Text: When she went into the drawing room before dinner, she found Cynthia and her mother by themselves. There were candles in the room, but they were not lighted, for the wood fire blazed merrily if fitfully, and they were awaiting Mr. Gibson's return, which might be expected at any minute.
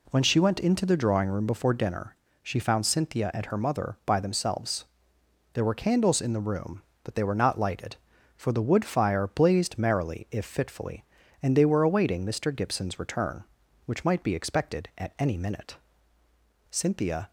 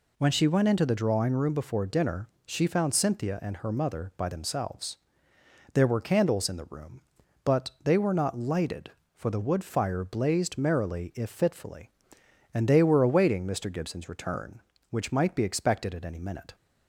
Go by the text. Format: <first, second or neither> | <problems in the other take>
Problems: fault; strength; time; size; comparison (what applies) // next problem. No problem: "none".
second | goes on to say "Cynthia"; from 16.7 s on; 0.60 s long